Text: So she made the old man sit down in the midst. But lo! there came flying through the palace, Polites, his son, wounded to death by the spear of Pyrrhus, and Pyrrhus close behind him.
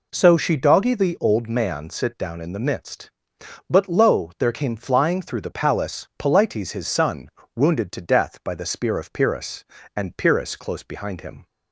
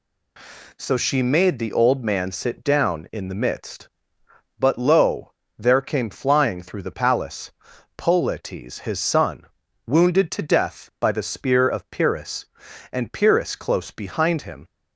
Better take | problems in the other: second | says "doggy" for "made"; at 0.5 s

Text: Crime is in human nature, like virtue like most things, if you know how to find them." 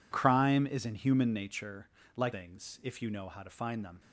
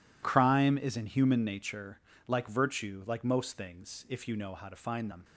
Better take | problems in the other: second | skips "virtue like most"; at 2.3 s

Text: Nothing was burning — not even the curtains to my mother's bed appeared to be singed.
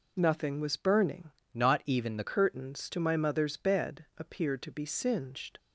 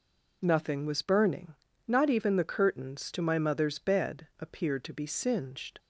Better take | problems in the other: second | changes voice from "not" to "the"; from 1.5 to 2.2 s; 0.7 s long

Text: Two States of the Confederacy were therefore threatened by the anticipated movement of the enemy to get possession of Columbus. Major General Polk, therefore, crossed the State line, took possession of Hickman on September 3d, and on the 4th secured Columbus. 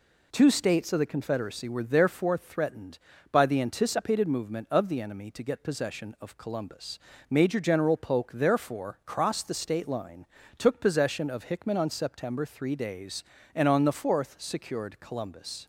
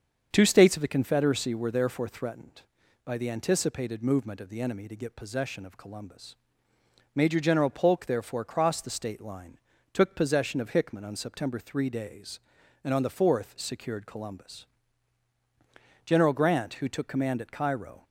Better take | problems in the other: first | starts louder than the rest; until 1.3 s; 7 dB // goes on to say "General Grant who took command at Cairo"; strong; from 16.0 s on; 1.9 s long

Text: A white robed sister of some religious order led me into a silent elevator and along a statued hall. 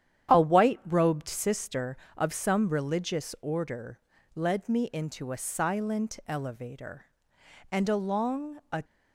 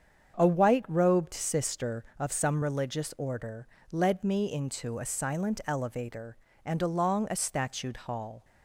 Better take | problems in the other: second | starts louder than the rest; strong; until 1.4 s; 9.5 dB; strong in the second // pauses between "order" and "led"; at 3.9 s; 0.38 s long; slight in the second // stops before "statued hall"; at 8.8 s

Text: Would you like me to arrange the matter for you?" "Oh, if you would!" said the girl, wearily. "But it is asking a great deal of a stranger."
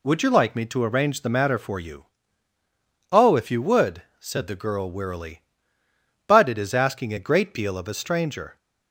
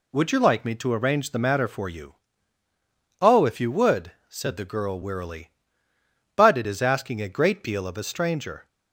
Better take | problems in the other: neither | none

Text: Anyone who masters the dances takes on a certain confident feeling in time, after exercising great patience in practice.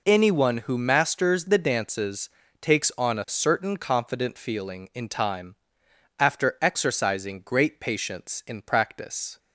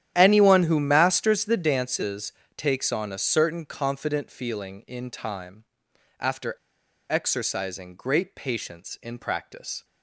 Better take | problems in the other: first | starts louder than the rest; strong; until 1.1 s; 10.5 dB // pauses between "dances" and "takes"; slight; at 2.3 s; 0.24 s long; slight in the first // pauses between "after" and "exercising"; noticeable; at 6.5 s; 0.56 s long

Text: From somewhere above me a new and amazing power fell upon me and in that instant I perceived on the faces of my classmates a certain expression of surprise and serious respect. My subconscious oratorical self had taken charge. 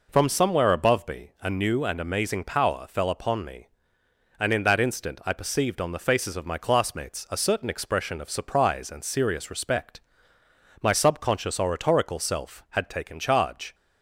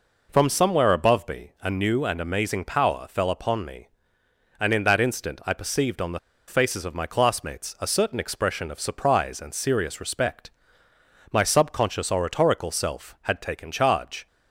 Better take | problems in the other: first | pauses between "the" and "faces"; slight; at 6.1 s; 0.29 s long

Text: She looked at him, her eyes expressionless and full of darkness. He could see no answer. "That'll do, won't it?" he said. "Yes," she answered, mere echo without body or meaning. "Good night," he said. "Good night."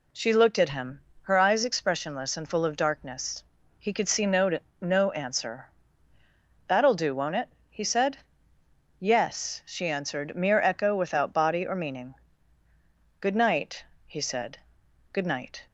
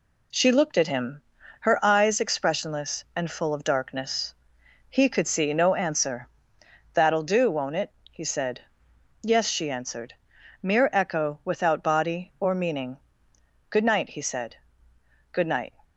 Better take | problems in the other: second | says "no" twice; at 4.8 s

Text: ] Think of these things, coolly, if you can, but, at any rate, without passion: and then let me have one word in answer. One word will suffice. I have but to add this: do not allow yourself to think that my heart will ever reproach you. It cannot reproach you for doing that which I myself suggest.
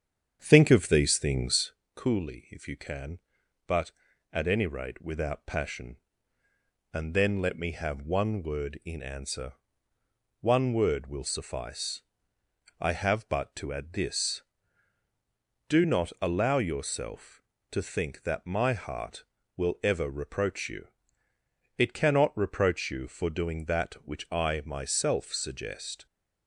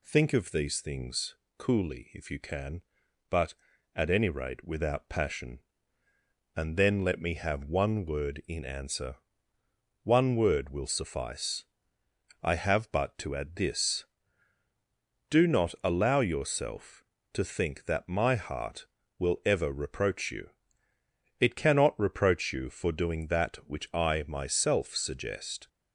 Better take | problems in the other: second | starts louder than the rest; strong; until 1.8 s; 8 dB

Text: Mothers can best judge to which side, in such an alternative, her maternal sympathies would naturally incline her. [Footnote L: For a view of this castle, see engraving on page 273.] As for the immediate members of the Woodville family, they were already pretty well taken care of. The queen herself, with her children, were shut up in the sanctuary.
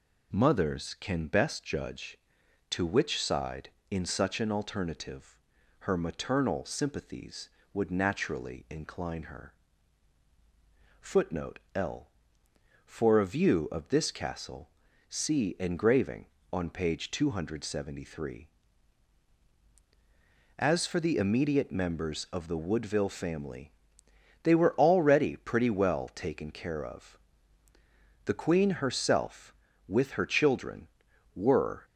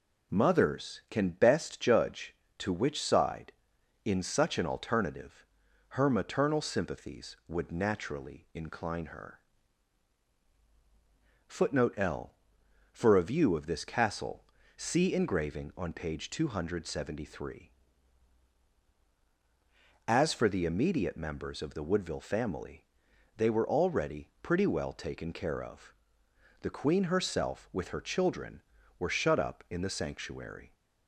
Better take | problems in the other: second | pauses between "Footnote" and "L"; slight; at 11.5 s; 0.16 s long // stops before "shut up in the sanctuary"; at 31.8 s

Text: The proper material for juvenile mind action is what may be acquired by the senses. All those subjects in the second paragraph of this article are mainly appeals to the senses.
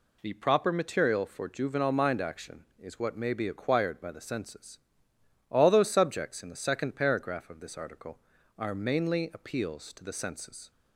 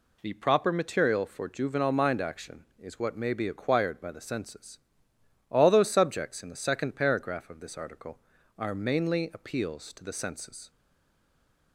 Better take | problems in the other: first | stays silent after the last word; from 10.7 s on; 1.0 s long

